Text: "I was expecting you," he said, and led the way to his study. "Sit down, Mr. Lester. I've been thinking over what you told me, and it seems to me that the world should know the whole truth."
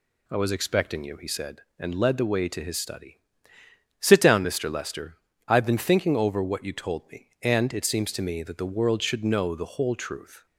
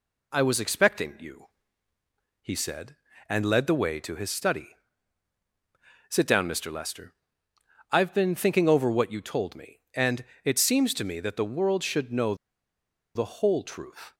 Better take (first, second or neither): first